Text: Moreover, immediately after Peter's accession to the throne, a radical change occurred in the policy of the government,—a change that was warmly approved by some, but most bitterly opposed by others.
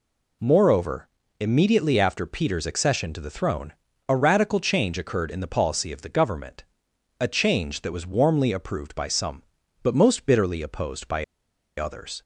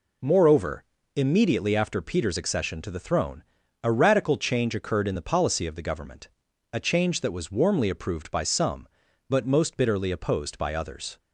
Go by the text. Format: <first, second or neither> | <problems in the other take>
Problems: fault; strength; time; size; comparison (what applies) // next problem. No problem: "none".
second | pauses between "by" and "others"; noticeable; at 11.2 s; 0.53 s long